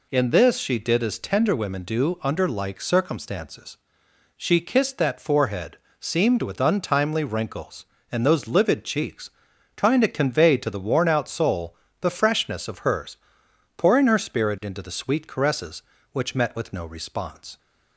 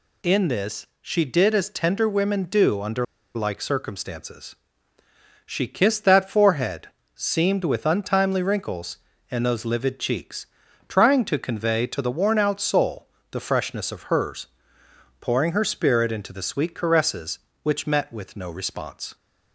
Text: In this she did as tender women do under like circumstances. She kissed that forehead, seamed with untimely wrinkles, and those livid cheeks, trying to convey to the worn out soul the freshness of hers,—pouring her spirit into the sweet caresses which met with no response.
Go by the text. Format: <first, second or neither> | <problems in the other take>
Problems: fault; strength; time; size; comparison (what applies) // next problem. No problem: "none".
first | pauses between "under" and "like"; slight; at 3.0 s; 0.30 s long // pauses between "soul" and "the"; slight; at 13.0 s; 0.24 s long; slight in the first